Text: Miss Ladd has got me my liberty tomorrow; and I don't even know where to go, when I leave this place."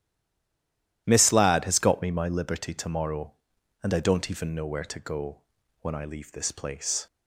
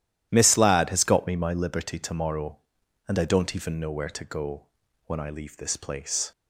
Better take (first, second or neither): second